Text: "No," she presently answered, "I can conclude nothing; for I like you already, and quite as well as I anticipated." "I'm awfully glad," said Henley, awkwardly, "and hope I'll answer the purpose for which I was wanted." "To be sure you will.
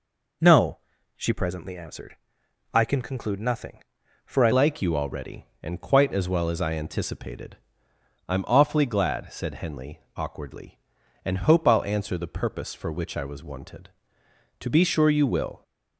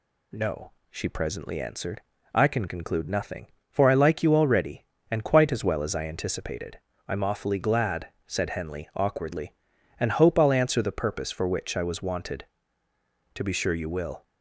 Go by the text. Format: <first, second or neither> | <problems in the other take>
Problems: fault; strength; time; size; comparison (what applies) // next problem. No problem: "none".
second | changes voice at "like"; from 4.5 s on; 11.1 s long